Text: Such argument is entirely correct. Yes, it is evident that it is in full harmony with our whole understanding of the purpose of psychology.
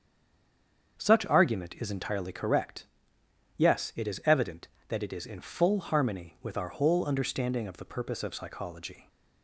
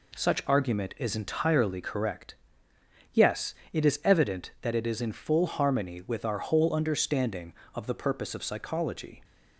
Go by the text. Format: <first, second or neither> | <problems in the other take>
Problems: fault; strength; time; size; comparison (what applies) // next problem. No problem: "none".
second | stays silent before the first word; until 0.9 s; 0.9 s long // starts louder than the rest; strong; until 2.0 s; 7 dB